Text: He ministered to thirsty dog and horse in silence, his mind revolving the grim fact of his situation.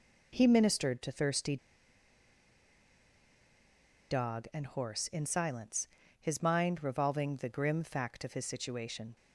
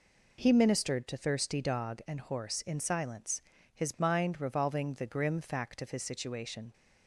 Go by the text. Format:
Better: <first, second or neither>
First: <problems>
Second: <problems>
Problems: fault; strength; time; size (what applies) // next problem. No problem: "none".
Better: second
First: pauses between "thirsty" and "dog"; strong; at 1.5 s; 2.5 s long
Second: none